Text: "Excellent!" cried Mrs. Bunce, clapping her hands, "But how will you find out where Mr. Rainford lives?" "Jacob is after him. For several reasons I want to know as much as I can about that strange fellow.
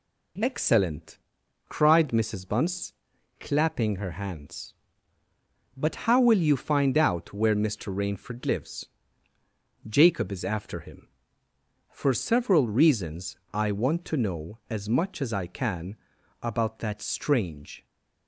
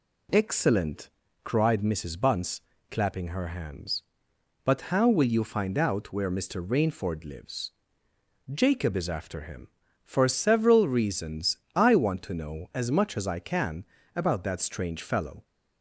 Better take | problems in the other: second | pauses between "reasons" and "I"; slight; at 13.3 s; 0.16 s long; slight in the second // pauses between "can" and "about"; noticeable; at 15.9 s; 0.46 s long; slight in the second // stops before "fellow"; at 17.8 s

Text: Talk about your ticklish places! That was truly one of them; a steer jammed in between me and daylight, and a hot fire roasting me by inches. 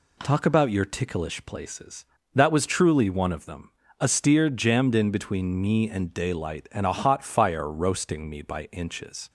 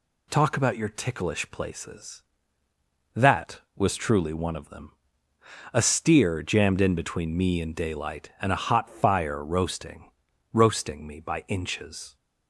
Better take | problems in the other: first | says "roasting" twice; at 10.5 s

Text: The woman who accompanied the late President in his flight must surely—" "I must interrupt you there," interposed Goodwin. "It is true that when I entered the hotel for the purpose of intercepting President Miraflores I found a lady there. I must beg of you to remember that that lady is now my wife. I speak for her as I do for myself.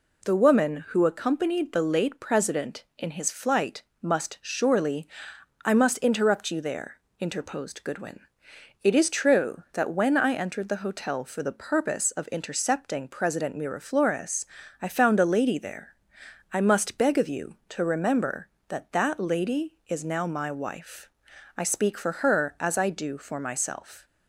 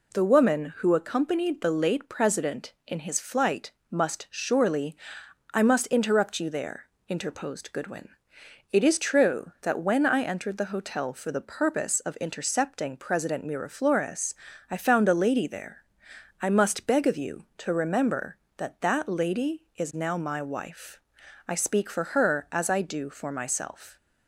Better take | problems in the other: neither | pauses between "flight" and "must"; slight; the same in both // pauses between "Miraflores" and "I"; the same in both

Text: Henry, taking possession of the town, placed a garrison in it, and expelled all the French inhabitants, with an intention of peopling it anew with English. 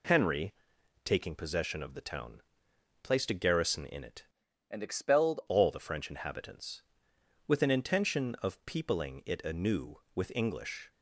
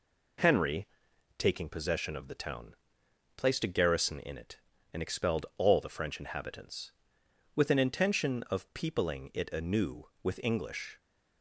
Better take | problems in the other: second | changes voice from "and" to "expelled"; from 4.7 to 5.4 s; 0.7 s long

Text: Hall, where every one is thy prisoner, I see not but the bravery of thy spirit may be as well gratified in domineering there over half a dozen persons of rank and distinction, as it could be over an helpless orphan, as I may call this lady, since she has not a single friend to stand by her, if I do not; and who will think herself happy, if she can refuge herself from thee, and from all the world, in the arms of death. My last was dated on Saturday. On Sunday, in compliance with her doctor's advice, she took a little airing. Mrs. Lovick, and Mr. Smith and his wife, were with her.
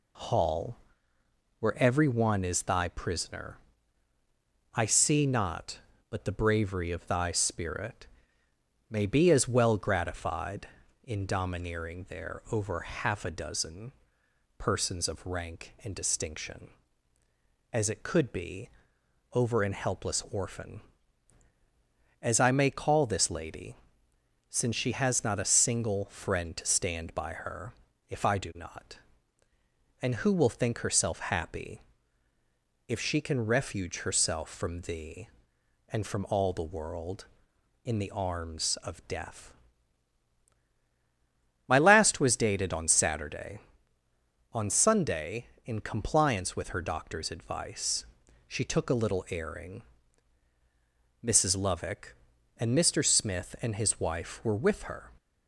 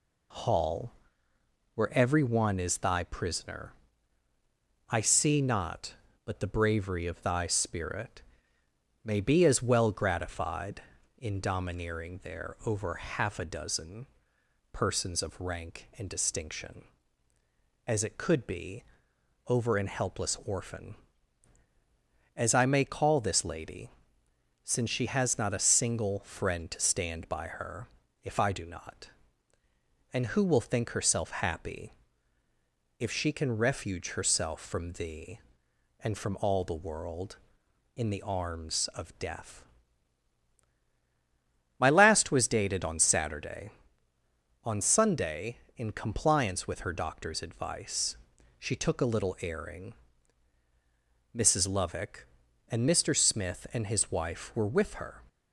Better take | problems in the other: neither | pauses between "spirit" and "may"; noticeable; the same in both // pauses between "dozen" and "persons"; noticeable; the same in both // pauses between "be" and "over"; noticeable; the same in both

